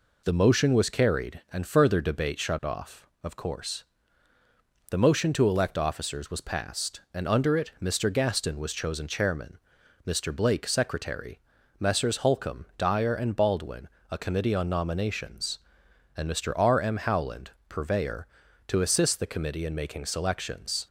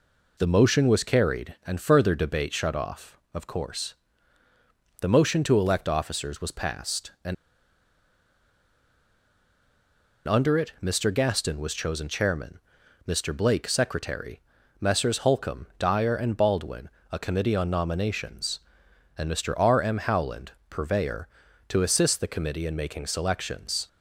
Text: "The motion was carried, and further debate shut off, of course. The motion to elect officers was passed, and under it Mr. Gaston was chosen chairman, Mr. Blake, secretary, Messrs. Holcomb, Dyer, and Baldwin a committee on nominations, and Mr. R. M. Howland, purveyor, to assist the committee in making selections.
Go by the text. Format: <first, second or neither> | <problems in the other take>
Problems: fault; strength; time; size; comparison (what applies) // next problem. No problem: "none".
first | pauses between "and" and "under"; strong; at 7.3 s; 2.9 s long // pauses between "Baldwin" and "a"; slight; at 16.8 s; 0.22 s long; slight in the first